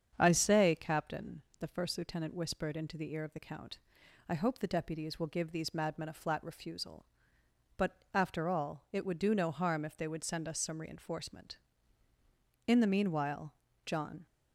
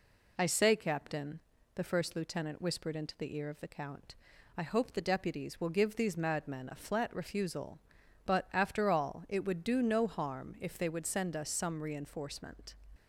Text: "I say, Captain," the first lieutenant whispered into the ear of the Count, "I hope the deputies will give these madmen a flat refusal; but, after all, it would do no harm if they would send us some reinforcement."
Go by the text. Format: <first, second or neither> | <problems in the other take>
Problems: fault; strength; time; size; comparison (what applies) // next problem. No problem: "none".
second | starts louder than the rest; strong; until 1.2 s; 7.5 dB // goes on to say "In the meanwhile John"; from 12.6 s on; 1.5 s long